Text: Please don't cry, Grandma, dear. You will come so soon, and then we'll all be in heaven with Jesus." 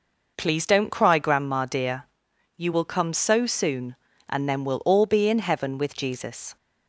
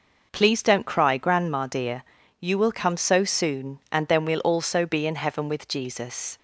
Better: first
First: none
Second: says "also" for "all"; at 4.4 s

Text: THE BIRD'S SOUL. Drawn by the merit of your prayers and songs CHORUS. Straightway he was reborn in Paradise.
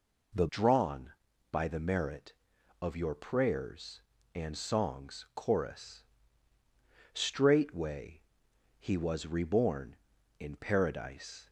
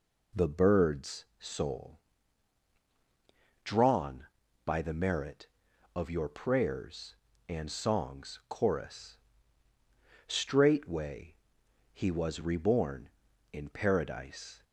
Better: second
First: skips "BIRD'S SOUL"; at 0.4 s // pauses between "Straightway" and "he"; noticeable; at 8.2 s; 0.56 s long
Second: pauses between "Straightway" and "he"; noticeable; at 11.3 s; 0.56 s long

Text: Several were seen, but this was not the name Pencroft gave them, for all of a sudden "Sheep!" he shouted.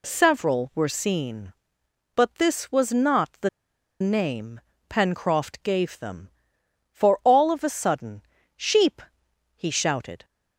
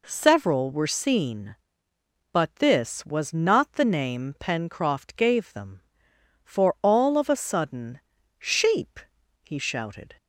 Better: second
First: pauses between "the" and "name"; noticeable; at 3.4 s; 0.51 s long // pauses between "name" and "Pencroft"; slight; at 4.6 s; 0.28 s long // pauses between "sudden" and "Sheep"; slight; at 8.2 s; 0.34 s long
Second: pauses between "sudden" and "Sheep"; at 8.0 s; 0.40 s long

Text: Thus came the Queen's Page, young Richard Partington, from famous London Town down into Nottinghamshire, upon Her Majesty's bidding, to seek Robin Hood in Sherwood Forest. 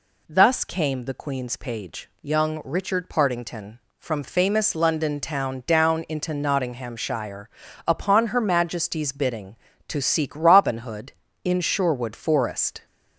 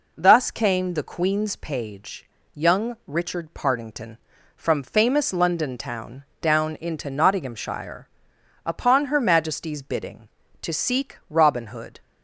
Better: first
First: none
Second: pauses between "Town" and "down"; slight; at 6.2 s; 0.18 s long // stops before "in Sherwood Forest"; at 12.0 s

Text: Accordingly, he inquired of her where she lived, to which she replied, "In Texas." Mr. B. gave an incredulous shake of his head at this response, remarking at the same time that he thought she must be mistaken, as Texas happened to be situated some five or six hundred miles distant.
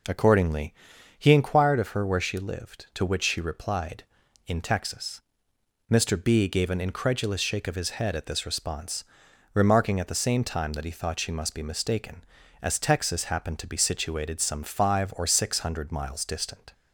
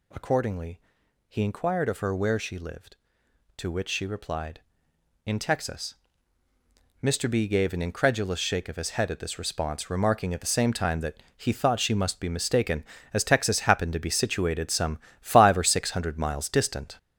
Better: first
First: none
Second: gets louder; noticeable; throughout; 6 dB // pauses between "that" and "he"; slight; at 11.1 s; 0.20 s long // pauses between "some" and "five"; slight; at 14.9 s; 0.20 s long

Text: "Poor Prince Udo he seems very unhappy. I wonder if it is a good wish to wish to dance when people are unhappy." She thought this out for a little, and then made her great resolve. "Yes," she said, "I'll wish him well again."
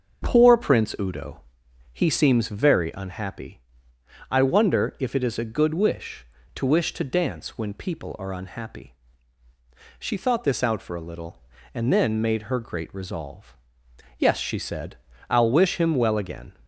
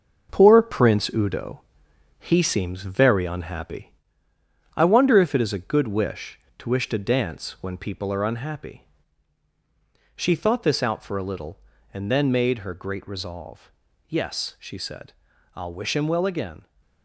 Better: first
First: starts louder than the rest; until 1.2 s; 6.5 dB // pauses between "Udo" and "he"; noticeable; at 1.4 s; 0.50 s long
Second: gets quieter; throughout; 6.5 dB // starts louder than the rest; noticeable; until 1.3 s; 6 dB // pauses between "Udo" and "he"; noticeable; at 1.6 s; 0.62 s long

